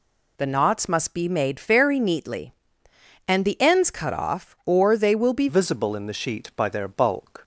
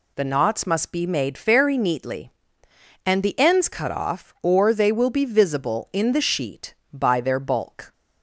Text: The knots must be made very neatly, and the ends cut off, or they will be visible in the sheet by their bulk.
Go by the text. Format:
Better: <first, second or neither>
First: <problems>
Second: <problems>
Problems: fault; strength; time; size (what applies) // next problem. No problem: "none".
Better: second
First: changes voice at "visible"; from 5.4 s on; 1.9 s long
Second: none